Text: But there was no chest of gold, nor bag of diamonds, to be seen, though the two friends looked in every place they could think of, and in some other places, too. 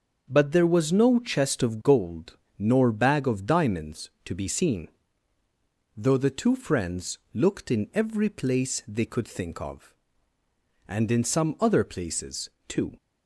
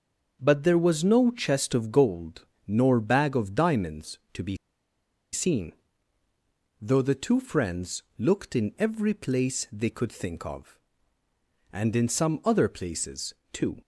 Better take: first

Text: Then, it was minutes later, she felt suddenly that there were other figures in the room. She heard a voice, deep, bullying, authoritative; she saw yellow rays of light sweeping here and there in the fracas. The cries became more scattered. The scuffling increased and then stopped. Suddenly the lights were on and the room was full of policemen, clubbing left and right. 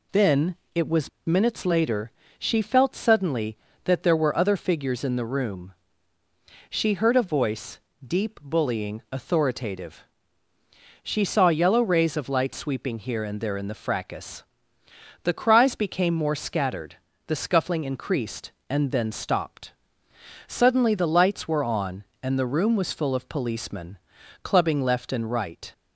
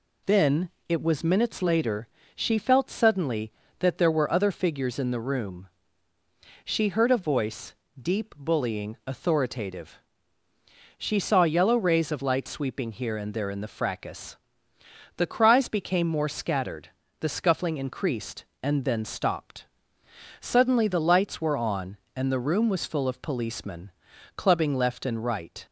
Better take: second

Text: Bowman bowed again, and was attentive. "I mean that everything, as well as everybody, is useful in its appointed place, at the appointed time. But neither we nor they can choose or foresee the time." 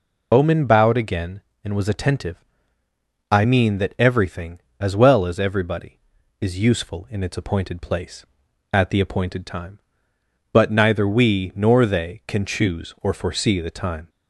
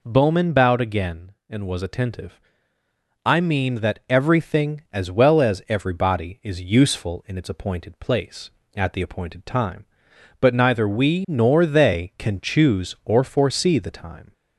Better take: second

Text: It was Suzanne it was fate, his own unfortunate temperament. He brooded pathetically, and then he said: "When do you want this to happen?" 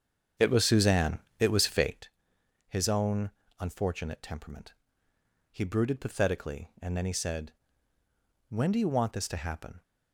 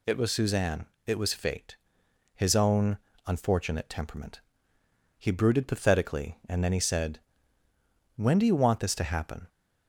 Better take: second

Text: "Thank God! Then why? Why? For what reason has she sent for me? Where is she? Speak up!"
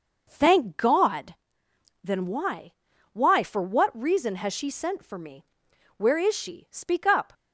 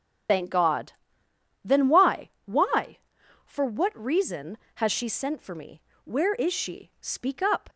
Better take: first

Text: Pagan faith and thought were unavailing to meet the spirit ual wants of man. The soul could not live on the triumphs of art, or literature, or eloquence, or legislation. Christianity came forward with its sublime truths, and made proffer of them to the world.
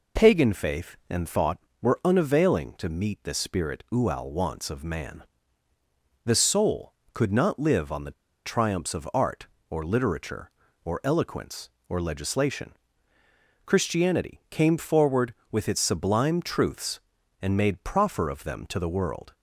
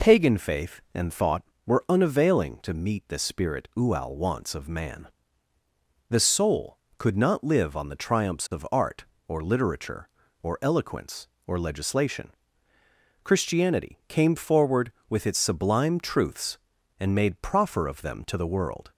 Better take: second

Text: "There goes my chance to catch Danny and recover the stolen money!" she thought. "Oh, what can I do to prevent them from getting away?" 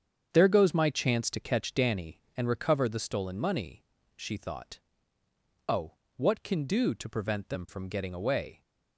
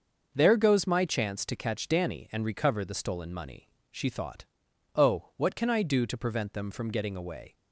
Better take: second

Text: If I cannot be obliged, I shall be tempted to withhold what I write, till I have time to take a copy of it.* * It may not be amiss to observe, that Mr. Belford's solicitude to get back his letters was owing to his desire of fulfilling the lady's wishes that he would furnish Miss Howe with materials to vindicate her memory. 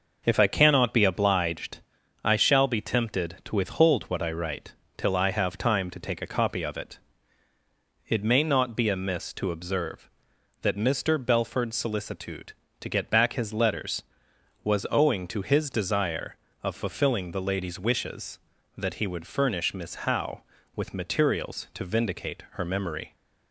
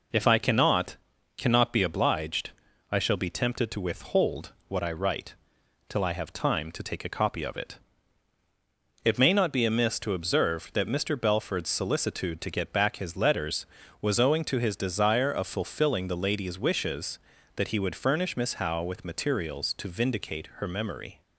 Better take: first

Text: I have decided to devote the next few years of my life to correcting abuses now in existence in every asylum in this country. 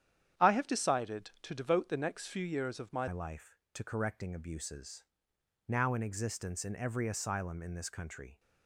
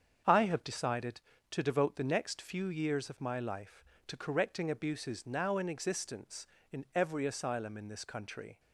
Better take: second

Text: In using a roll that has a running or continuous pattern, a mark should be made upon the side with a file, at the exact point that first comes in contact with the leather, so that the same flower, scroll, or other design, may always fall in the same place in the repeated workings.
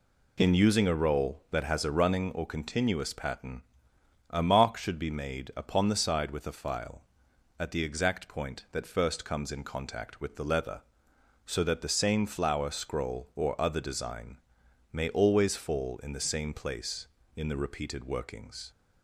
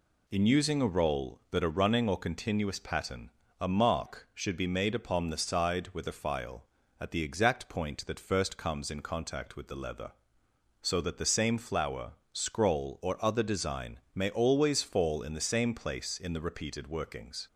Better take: first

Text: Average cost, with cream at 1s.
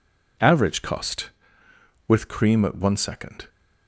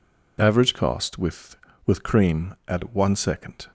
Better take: first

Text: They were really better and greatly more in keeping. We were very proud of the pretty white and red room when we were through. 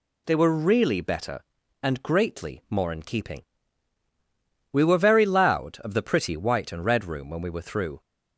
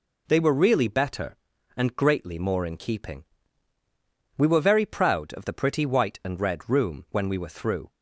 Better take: second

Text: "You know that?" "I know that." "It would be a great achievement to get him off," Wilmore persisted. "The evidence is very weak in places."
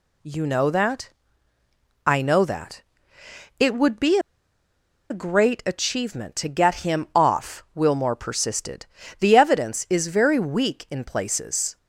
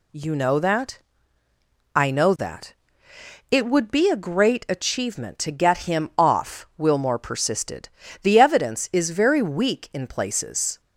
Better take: second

